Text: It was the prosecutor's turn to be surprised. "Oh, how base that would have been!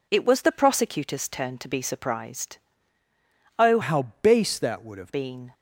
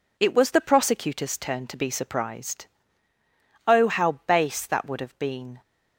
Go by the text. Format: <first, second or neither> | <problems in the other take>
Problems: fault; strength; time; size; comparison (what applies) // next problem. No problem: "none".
second | changes voice from "how" to "have"; from 3.8 to 5.1 s; 1.3 s long